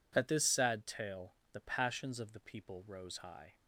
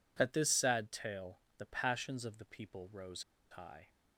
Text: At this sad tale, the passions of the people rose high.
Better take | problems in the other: first | pauses between "rose" and "high"; slight; at 3.2 s; 0.27 s long

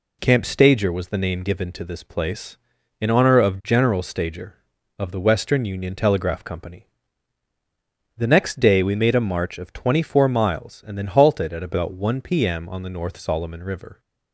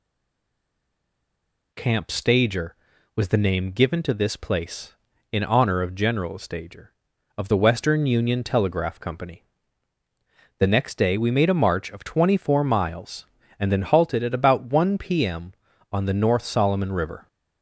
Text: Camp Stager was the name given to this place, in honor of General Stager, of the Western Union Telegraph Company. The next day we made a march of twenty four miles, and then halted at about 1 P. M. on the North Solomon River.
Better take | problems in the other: first | stays silent before the first word; noticeable; until 1.7 s; 1.7 s long

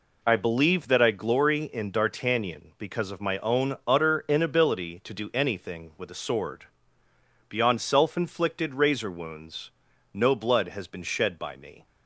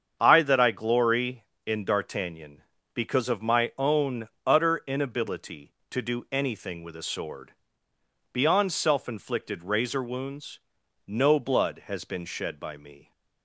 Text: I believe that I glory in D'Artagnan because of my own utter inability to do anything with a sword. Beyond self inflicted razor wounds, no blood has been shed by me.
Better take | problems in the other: first | starts louder than the rest; strong; until 1.2 s; 7.5 dB // skips "believe"; at 0.4 s // pauses between "own" and "utter"; slight; at 4.2 s; 0.16 s long

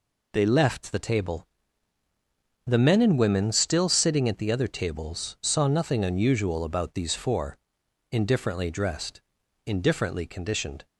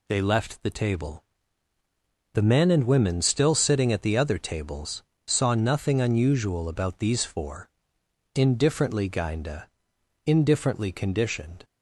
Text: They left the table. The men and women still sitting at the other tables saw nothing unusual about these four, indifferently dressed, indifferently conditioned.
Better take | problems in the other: first | pauses between "tables" and "saw"; slight; at 5.0 s; 0.24 s long // says "gainda" for "dressed"; at 9.0 s

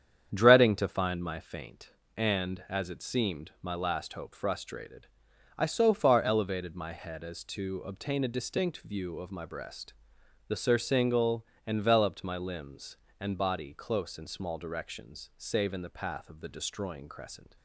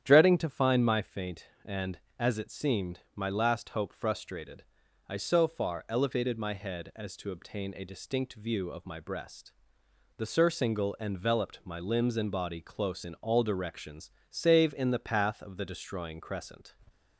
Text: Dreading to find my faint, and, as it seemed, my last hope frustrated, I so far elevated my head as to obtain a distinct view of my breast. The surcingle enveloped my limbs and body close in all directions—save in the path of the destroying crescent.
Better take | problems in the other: second | starts louder than the rest; strong; until 1.3 s; 8.5 dB; strong in the second // pauses between "surcingle" and "enveloped"; slight; at 11.4 s; 0.18 s long // says "small" for "all"; at 14.2 s

